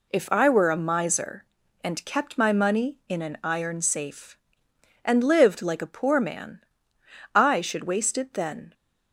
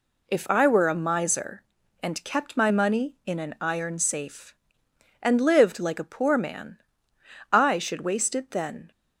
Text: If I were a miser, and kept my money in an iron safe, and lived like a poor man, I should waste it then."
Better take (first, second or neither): neither